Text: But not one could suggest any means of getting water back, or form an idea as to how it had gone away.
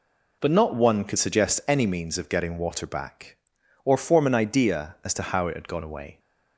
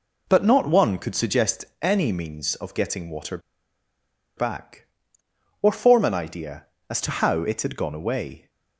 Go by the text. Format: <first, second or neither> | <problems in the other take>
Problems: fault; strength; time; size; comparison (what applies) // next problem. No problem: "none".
first | pauses between "suggest" and "any"; slight; at 1.6 s; 0.16 s long // pauses between "water" and "back"; at 3.3 s; 0.98 s long